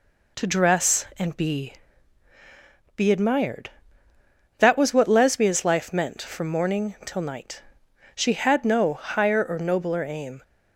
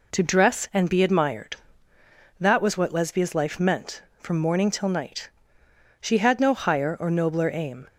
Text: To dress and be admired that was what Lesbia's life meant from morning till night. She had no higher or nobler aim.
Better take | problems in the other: second | says "be" twice; at 2.9 s

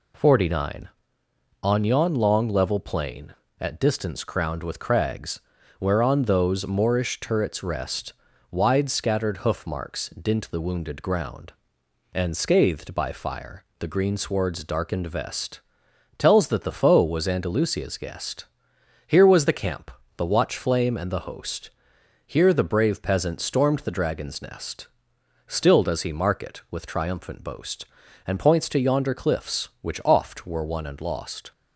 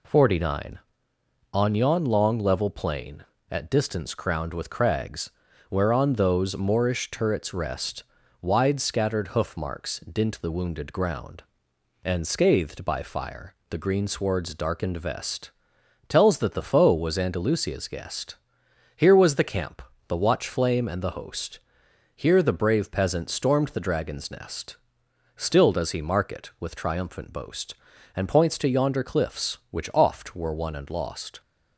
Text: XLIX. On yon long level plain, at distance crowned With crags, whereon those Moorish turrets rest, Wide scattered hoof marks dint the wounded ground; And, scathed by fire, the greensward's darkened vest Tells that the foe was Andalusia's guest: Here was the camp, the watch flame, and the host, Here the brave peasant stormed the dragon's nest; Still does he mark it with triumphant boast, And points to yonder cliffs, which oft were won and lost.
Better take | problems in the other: neither | pauses between "vest" and "Tells"; noticeable; the same in both

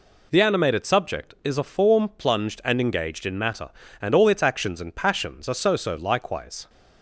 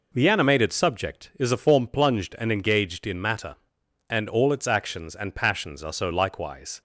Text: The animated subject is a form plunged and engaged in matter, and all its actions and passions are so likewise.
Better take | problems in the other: second | says "so" twice; at 5.7 s

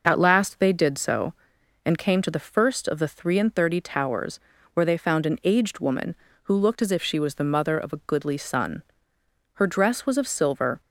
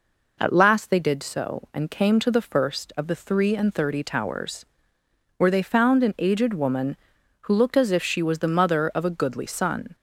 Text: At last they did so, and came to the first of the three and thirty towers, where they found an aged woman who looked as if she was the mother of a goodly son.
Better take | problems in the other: second | goes on to say "Her dress was of silver"; noticeable; from 9.5 s on; 1.2 s long

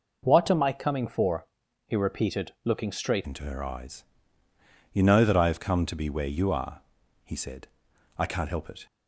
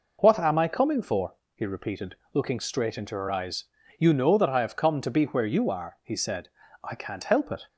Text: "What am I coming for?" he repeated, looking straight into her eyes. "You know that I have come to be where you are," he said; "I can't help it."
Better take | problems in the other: second | changes voice at "into"; from 3.2 s on; 5.6 s long

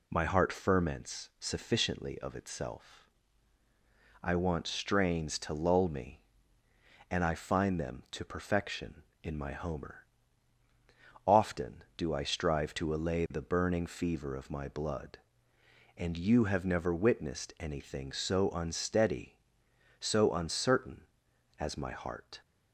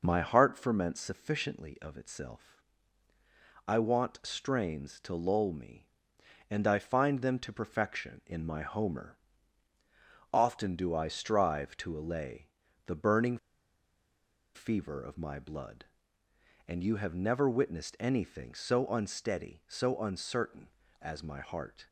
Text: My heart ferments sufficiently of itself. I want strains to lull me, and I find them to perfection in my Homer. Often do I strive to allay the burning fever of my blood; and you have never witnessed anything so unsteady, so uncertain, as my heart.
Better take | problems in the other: first | pauses between "allay" and "the"; at 12.4 s; 0.38 s long // pauses between "burning" and "fever"; at 13.3 s; 1.1 s long

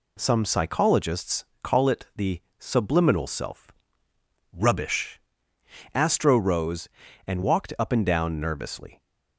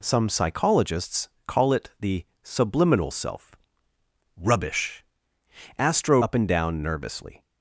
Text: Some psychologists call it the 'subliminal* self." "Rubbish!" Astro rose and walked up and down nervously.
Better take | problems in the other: first | pauses between "psychologists" and "call"; slight; at 1.2 s; 0.18 s long; slight in the first // pauses between "the" and "subliminal"; slight; at 2.2 s; 0.16 s long; slight in the first // skips "rose and walked"; at 6.2 s

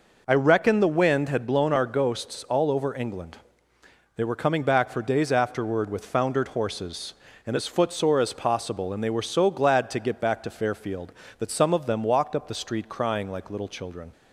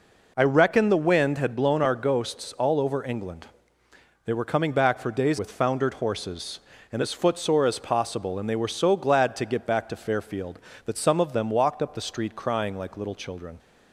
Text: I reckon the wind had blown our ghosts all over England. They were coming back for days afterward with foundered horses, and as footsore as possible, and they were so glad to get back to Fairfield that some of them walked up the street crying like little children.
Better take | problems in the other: first | skips "afterward"; at 5.3 s

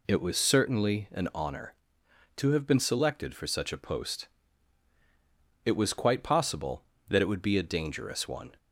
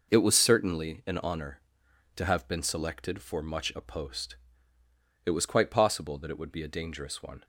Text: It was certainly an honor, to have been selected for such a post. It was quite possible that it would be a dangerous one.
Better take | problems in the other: first | says "much" for "such"; at 3.4 s

